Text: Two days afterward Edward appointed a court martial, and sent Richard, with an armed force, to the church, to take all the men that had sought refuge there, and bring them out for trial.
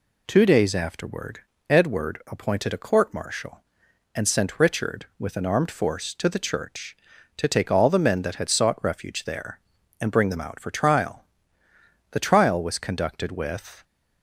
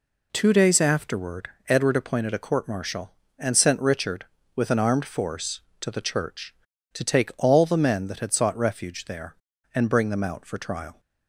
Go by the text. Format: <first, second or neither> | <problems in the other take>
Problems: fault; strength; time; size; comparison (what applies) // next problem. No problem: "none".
second | pauses between "afterward" and "Edward"; slight; at 1.3 s; 0.30 s long; slight in the second // goes on to say "The trial was conducted with"; strong; from 12.1 s on; 1.7 s long